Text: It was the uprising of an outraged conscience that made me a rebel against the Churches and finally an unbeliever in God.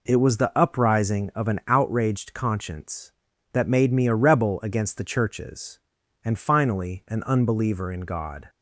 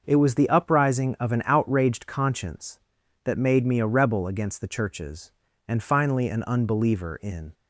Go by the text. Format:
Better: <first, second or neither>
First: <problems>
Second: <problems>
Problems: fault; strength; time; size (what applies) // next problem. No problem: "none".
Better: first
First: none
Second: starts louder than the rest; until 1.0 s; 6.5 dB // stops before "God"; at 7.5 s